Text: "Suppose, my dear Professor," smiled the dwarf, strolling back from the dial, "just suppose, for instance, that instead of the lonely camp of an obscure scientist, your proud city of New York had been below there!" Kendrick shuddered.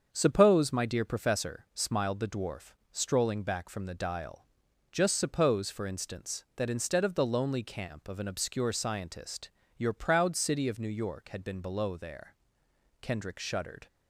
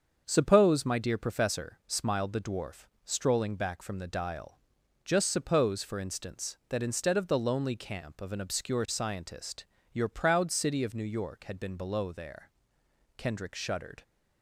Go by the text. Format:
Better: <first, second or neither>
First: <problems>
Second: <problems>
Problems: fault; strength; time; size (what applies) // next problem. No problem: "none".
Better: neither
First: starts louder than the rest; until 1.1 s; 7 dB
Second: starts louder than the rest; until 1.2 s; 7 dB